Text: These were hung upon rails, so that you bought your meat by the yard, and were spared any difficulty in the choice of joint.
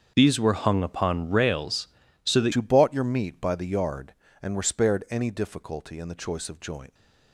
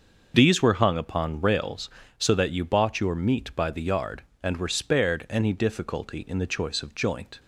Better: second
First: starts louder than the rest; until 1.1 s; 7 dB // changes voice at "you"; from 2.5 s on; 4.4 s long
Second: starts louder than the rest; until 1.3 s; 6.5 dB

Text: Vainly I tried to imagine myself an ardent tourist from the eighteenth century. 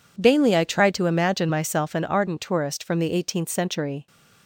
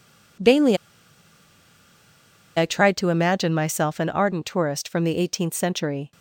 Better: first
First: none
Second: pauses between "Vainly" and "I"; strong; at 0.7 s; 1.8 s long

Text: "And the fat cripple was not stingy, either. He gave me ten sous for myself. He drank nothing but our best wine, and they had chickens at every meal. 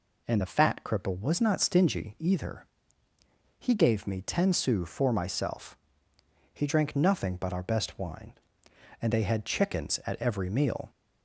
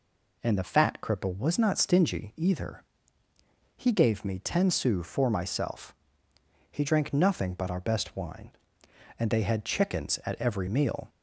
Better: neither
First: none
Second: none

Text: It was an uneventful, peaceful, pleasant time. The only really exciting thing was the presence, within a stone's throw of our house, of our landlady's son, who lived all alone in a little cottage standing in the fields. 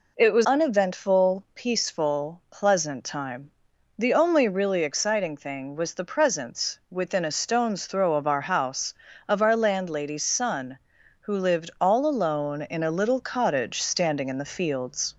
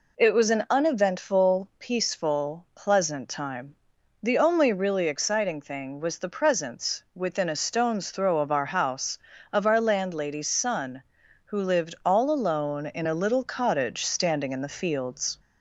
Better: second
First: skips "an"; at 0.4 s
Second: none

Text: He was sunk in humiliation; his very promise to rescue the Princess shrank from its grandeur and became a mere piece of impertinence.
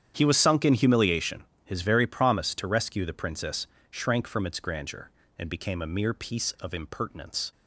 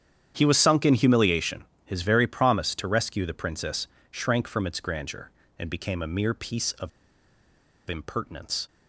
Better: first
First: starts louder than the rest; strong; until 1.1 s; 9 dB // pauses between "Princess" and "shrank"; slight; at 3.6 s; 0.24 s long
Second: starts louder than the rest; strong; until 1.3 s; 9 dB // pauses between "Princess" and "shrank"; slight; at 3.8 s; 0.24 s long // pauses between "of" and "impertinence"; at 6.8 s; 0.99 s long

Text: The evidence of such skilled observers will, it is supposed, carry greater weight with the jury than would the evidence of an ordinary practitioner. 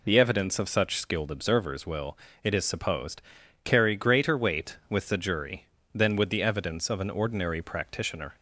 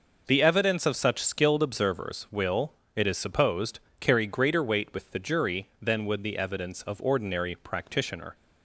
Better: first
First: none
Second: skips "an"; at 7.0 s

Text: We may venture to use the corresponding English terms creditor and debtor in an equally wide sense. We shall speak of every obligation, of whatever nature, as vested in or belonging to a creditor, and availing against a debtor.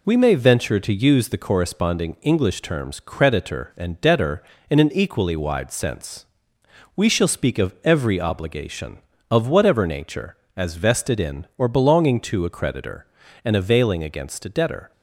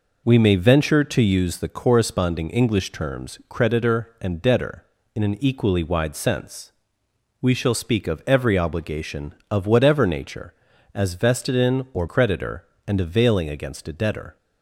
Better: first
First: none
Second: skips "belonging to a"; at 12.0 s

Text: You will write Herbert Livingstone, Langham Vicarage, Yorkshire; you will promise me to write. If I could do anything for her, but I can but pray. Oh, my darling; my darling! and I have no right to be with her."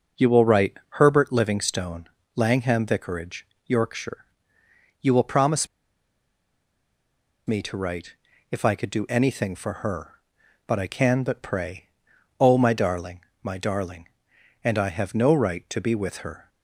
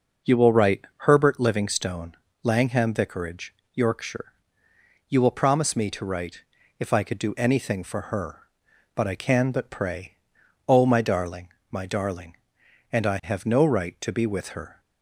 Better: second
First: pauses between "promise" and "me"; strong; at 5.6 s; 1.7 s long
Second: none

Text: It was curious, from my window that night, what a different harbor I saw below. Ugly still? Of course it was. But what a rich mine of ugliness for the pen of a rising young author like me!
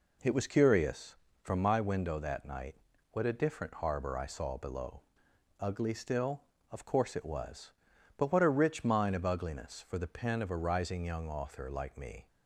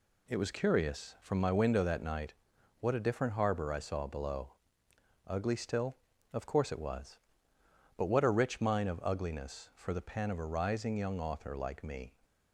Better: neither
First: none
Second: none

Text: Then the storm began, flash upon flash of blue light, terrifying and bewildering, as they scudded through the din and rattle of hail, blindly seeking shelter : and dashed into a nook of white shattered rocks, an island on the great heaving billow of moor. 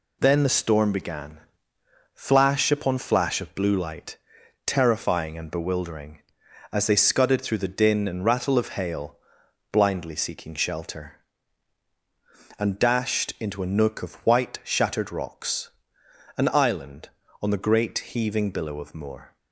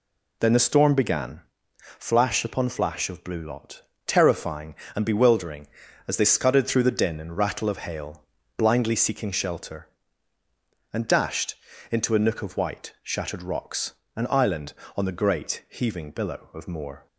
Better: first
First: none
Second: says "lot" for "light"; at 3.4 s // pauses between "dashed" and "into"; slight; at 11.5 s; 0.34 s long

